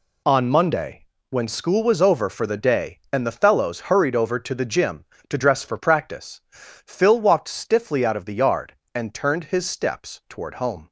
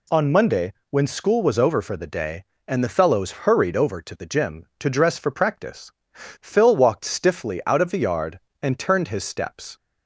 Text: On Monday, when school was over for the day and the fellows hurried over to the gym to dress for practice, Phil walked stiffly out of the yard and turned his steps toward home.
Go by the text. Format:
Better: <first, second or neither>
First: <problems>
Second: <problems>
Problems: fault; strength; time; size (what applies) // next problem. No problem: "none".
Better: first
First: none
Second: stops before "toward home"; at 9.7 s